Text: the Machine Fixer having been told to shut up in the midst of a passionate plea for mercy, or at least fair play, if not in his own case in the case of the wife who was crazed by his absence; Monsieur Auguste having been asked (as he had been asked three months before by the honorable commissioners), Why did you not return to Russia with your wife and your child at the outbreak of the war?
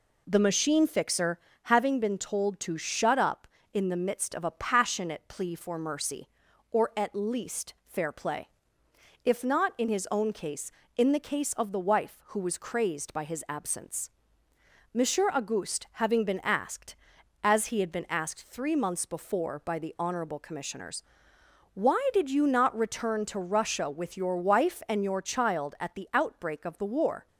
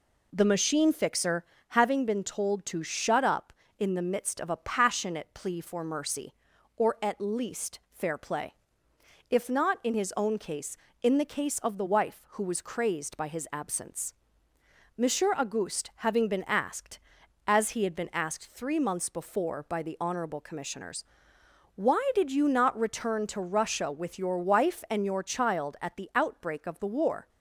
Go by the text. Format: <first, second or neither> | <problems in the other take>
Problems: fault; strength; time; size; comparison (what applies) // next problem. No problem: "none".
neither | pauses between "Fixer" and "having"; slight; the same in both